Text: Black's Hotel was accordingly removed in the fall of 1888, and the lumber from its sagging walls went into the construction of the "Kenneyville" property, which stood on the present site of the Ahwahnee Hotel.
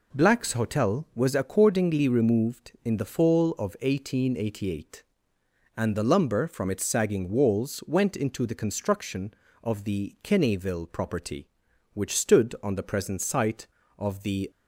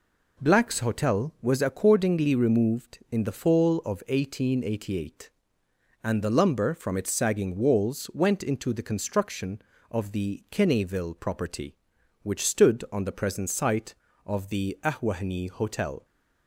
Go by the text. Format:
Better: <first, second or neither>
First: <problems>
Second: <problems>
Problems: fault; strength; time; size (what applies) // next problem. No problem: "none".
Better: second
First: stops before "Ahwahnee Hotel"; at 14.5 s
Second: none